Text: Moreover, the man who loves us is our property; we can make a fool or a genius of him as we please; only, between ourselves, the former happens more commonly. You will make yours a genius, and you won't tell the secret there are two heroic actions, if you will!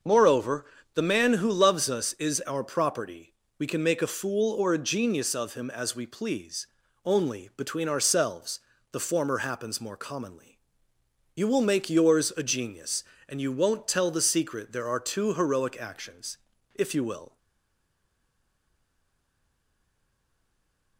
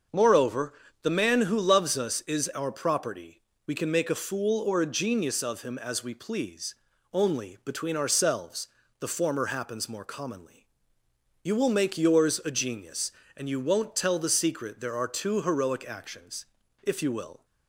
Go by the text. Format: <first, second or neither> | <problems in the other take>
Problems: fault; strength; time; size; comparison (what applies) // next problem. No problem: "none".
second | starts louder than the rest; until 1.3 s; 6.5 dB; also in the second // stays silent after the last word; strong; from 17.3 s on; 3.6 s long